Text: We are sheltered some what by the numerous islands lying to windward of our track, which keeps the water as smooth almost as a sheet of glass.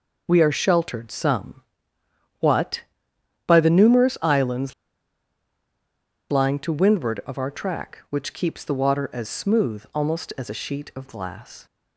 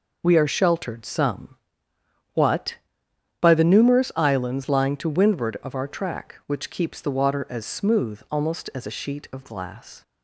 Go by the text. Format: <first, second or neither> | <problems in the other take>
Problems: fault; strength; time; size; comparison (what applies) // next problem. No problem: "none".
second | pauses between "some" and "what"; noticeable; at 1.6 s; 0.78 s long; noticeable in the second // pauses between "islands" and "lying"; strong; at 4.7 s; 1.5 s long